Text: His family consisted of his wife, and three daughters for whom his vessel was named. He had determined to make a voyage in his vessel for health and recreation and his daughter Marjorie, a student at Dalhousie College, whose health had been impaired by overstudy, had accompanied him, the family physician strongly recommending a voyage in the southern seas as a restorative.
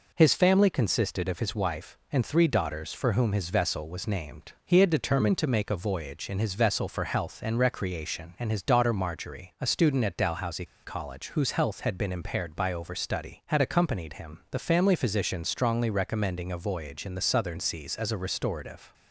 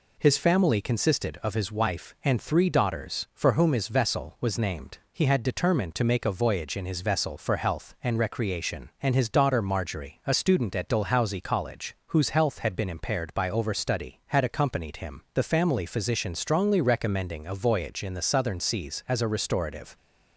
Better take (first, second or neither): second